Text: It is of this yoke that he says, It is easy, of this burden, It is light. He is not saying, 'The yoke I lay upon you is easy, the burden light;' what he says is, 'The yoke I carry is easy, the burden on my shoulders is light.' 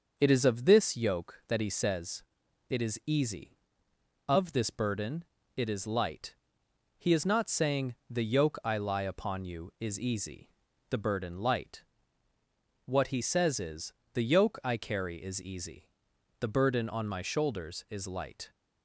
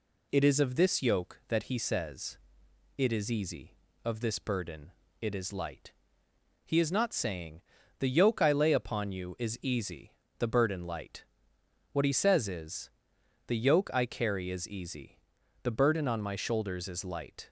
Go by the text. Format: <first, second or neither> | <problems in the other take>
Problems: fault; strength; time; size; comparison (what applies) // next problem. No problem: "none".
second | starts louder than the rest; until 1.1 s; 6 dB // says "lie" for "lay"; at 8.7 s